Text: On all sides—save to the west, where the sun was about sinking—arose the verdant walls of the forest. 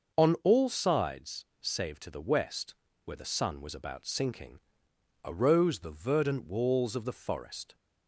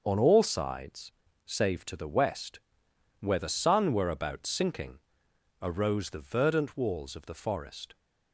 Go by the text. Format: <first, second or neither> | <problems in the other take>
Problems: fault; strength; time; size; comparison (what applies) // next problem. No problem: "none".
first | starts louder than the rest; until 1.0 s; 6 dB; noticeable in the first // says "were" for "was"; at 3.9 s